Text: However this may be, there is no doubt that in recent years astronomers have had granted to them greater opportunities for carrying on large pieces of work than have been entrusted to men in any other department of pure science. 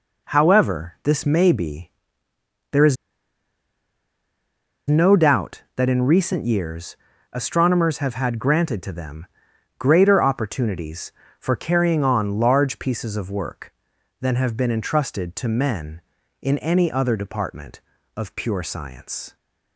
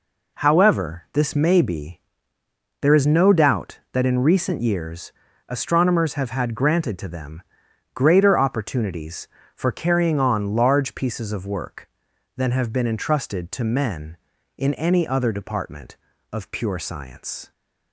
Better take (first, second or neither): second